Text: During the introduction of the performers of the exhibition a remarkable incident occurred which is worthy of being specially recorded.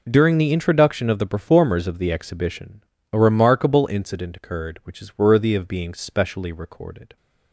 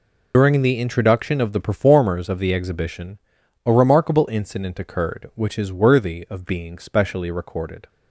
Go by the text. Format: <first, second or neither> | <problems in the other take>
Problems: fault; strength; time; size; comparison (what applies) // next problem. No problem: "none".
first | loses the start of "During"; at 0.3 s; 85 ms // pauses between "exhibition" and "a"; at 3.1 s; 0.44 s long; slight in the first